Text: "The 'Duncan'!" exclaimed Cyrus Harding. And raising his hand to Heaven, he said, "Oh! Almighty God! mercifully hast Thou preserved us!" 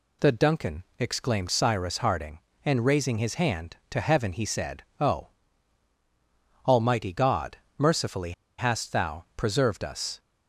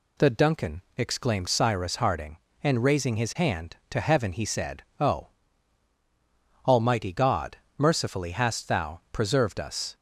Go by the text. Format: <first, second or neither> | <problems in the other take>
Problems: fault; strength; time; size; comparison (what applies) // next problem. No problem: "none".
second | pauses between "mercifully" and "hast"; slight; at 8.3 s; 0.25 s long